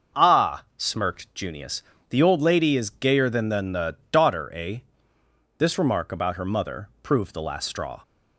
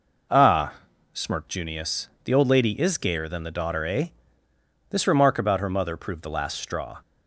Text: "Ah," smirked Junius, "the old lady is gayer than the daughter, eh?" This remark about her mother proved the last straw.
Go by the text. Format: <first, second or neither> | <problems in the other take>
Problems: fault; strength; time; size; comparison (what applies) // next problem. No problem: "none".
second | starts louder than the rest; until 1.2 s; 6.5 dB // says "than" twice; at 3.4 s